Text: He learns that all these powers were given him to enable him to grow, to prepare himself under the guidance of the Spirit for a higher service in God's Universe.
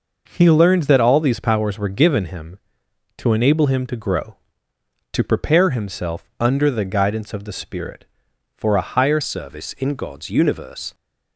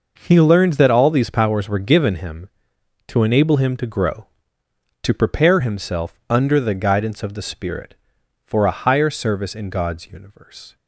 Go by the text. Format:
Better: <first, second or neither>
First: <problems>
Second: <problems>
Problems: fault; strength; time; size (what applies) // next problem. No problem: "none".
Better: second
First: changes voice at "service"; from 9.2 s on; 1.7 s long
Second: none